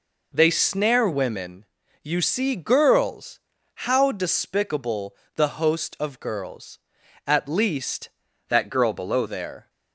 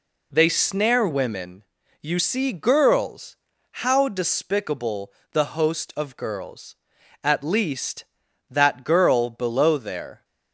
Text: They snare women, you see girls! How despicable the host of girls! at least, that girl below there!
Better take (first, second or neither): second